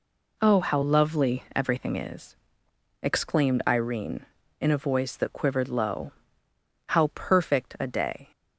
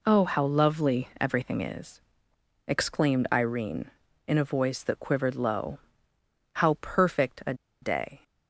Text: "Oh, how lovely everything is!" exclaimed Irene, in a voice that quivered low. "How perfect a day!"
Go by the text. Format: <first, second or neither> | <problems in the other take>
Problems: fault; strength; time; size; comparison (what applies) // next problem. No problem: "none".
first | pauses between "a" and "day"; slight; at 7.5 s; 0.28 s long